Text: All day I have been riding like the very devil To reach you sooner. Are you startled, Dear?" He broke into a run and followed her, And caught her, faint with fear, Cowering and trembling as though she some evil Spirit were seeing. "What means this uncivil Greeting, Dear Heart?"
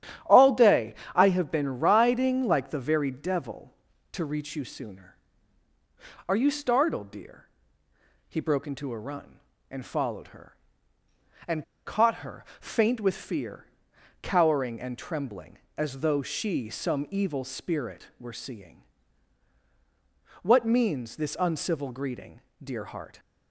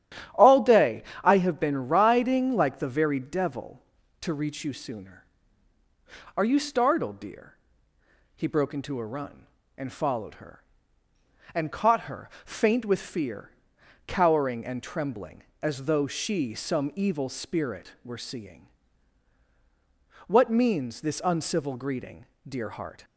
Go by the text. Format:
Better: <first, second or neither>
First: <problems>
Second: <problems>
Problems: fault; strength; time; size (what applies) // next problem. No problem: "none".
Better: second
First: starts louder than the rest; strong; until 1.4 s; 10.5 dB // pauses between "day" and "I"; slight; at 0.9 s; 0.20 s long // pauses between "And" and "caught"; slight; at 11.6 s; 0.21 s long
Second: starts louder than the rest; strong; until 1.5 s; 10.5 dB // pauses between "day" and "I"; slight; at 1.0 s; 0.20 s long